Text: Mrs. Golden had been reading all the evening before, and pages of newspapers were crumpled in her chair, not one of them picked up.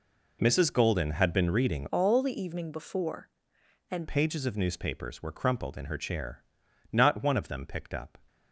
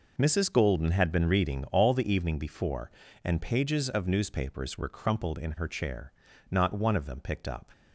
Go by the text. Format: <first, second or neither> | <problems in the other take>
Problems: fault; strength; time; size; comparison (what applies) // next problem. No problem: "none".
second | changes voice from "all" to "and"; from 1.9 to 4.0 s; 2.1 s long